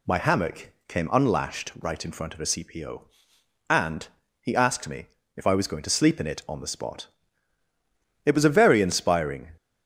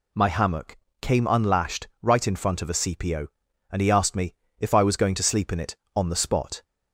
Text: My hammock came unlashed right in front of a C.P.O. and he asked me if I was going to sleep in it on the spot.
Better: second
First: pauses between "hammock" and "came"; slight; at 0.7 s; 0.16 s long // pauses between "and" and "he"; slight; at 4.0 s; 0.34 s long // pauses between "me" and "if"; slight; at 5.0 s; 0.28 s long // goes on to say "It was a very inspiring"; from 8.2 s on; 1.3 s long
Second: pauses between "hammock" and "came"; slight; at 0.7 s; 0.26 s long // pauses between "me" and "if"; slight; at 4.3 s; 0.24 s long

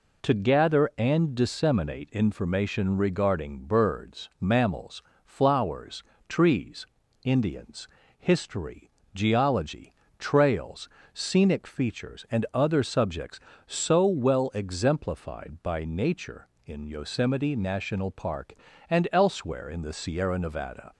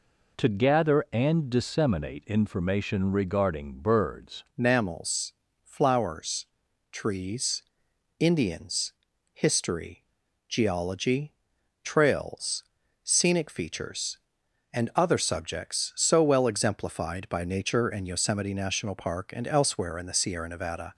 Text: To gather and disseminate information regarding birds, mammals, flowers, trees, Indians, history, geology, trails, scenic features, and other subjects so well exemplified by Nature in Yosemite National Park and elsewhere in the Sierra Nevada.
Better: first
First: none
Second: changes voice at "mammals"; from 4.5 s on; 16.4 s long

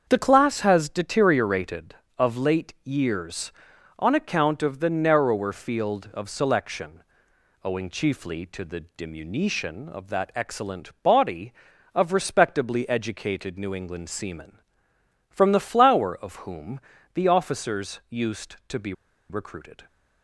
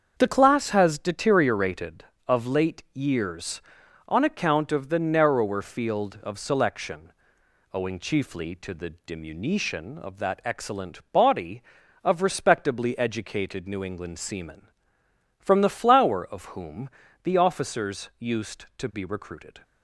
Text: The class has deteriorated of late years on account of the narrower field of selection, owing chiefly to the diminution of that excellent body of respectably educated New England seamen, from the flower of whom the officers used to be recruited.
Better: second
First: starts louder than the rest; until 1.1 s; 7 dB // pauses between "whom" and "the"; slight; at 16.7 s; 0.34 s long // pauses between "be" and "recruited"; at 18.9 s; 0.36 s long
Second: starts louder than the rest; until 1.1 s; 7 dB // pauses between "whom" and "the"; slight; at 16.8 s; 0.34 s long

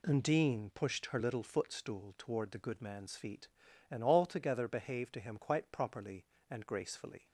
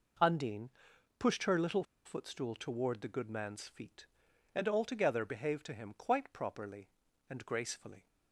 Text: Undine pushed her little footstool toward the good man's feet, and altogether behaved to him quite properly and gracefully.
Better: first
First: none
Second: pauses between "Undine" and "pushed"; noticeable; at 0.6 s; 0.50 s long // pauses between "little" and "footstool"; slight; at 1.8 s; 0.21 s long

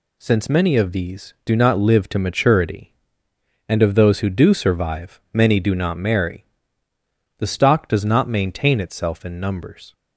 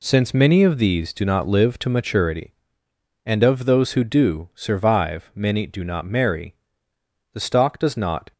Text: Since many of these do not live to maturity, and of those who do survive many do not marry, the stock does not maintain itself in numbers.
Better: first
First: none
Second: stops before "maintain itself in numbers"; at 8.3 s

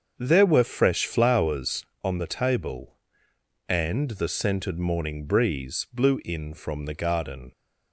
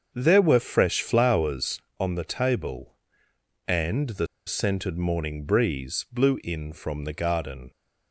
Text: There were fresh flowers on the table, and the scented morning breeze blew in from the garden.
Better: first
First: starts louder than the rest; until 1.1 s; 6.5 dB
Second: starts louder than the rest; until 1.1 s; 7 dB // pauses between "the" and "scented"; slight; at 4.2 s; 0.20 s long

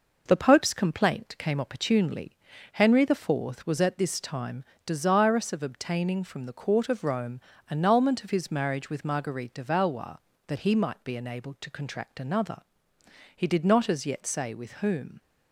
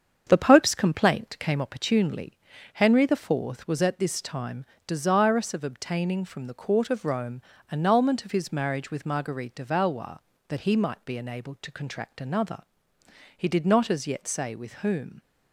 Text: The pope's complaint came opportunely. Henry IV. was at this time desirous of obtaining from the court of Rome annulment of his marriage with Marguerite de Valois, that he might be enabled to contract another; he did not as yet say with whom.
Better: first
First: pauses between "time" and "desirous"; slight; at 4.6 s; 0.20 s long // pauses between "Rome" and "annulment"; slight; at 7.3 s; 0.32 s long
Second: starts louder than the rest; strong; until 1.6 s; 7.5 dB // pauses between "time" and "desirous"; slight; at 4.6 s; 0.20 s long // pauses between "Rome" and "annulment"; slight; at 7.3 s; 0.32 s long

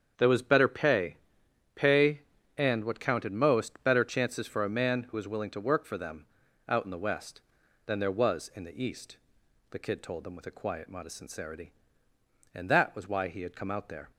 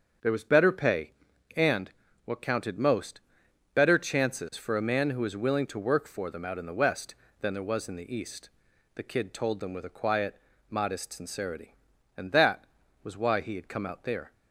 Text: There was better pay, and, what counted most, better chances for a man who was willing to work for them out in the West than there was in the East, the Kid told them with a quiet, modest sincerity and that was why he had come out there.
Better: second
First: starts louder than the rest; strong; until 1.1 s; 7.5 dB // says "pay" twice; at 1.7 s // pauses between "them" and "out"; at 6.2 s; 0.42 s long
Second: starts louder than the rest; until 1.6 s; 7 dB

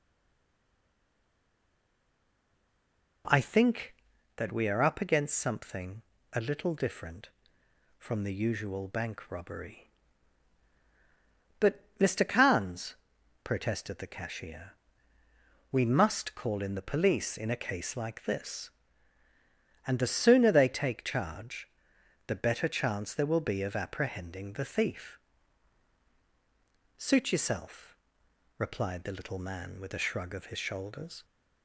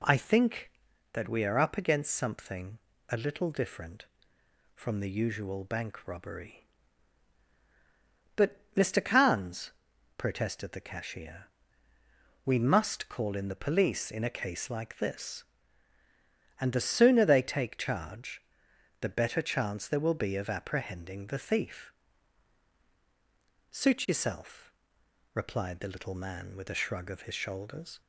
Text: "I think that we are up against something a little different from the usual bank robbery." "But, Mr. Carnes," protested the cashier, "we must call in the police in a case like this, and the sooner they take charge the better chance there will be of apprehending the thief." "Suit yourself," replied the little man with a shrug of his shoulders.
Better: second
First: stays silent before the first word; strong; until 3.2 s; 3.2 s long // pauses between "something" and "a"; slight; at 6.0 s; 0.30 s long // pauses between "charge" and "the"; noticeable; at 21.6 s; 0.56 s long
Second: pauses between "something" and "a"; slight; at 2.7 s; 0.30 s long // pauses between "charge" and "the"; noticeable; at 18.4 s; 0.56 s long

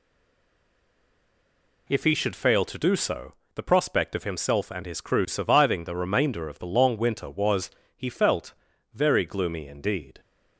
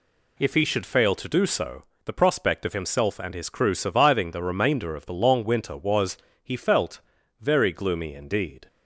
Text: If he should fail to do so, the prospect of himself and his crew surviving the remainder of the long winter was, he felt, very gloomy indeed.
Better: second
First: stays silent before the first word; noticeable; until 1.8 s; 1.8 s long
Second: none

